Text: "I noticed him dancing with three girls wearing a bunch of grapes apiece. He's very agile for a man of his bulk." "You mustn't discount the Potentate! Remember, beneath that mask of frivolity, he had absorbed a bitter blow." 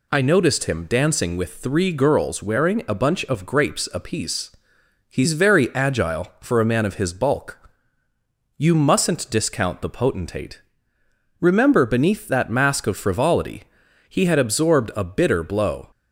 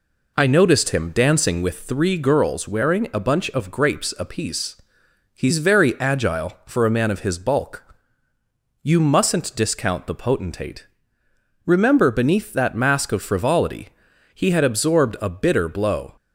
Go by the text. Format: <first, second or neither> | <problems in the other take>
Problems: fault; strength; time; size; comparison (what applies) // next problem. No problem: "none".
first | starts louder than the rest; until 2.0 s; 3.5 dB